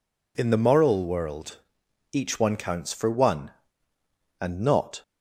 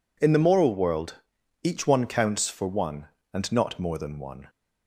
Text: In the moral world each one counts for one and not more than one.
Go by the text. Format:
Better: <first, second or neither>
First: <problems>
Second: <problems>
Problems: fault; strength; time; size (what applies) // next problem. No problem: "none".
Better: second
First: pauses between "world" and "each"; noticeable; at 1.5 s; 0.56 s long // stops before "more than one"; at 5.0 s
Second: pauses between "world" and "each"; noticeable; at 1.1 s; 0.48 s long